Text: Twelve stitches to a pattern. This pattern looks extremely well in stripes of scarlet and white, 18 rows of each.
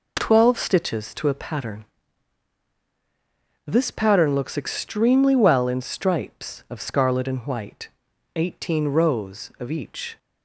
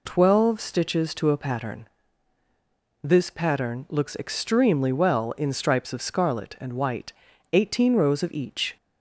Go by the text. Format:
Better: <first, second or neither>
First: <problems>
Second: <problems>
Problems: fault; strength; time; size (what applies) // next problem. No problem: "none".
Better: neither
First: none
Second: none